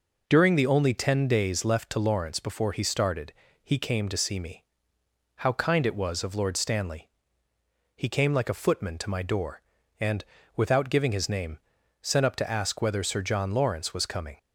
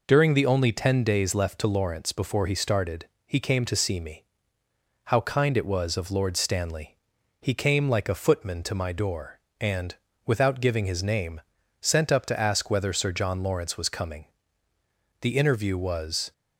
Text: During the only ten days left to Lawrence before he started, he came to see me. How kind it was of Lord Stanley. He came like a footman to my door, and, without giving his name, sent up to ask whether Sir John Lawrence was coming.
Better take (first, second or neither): first